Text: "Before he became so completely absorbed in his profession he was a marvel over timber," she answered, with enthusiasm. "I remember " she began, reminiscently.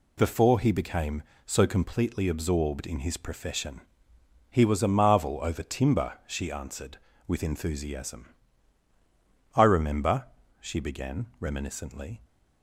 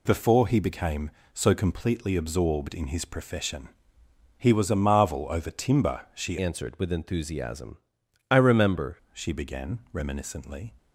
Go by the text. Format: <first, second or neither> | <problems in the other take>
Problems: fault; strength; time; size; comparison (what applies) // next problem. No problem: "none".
first | pauses between "profession" and "he"; noticeable; at 3.7 s; 0.68 s long; noticeable in the first // changes voice from "answered" to "remember"; from 6.4 to 8.9 s; 2.5 s long